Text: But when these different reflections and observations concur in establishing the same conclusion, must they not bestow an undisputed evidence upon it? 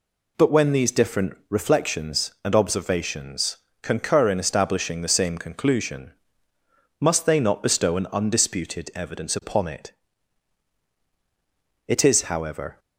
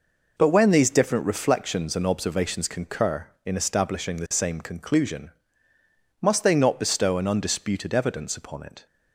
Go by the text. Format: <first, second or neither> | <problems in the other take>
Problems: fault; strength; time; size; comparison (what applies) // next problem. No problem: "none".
second | pauses between "observations" and "concur"; slight; at 3.5 s; 0.24 s long // goes on to say "It is however"; noticeable; from 11.8 s on; 0.92 s long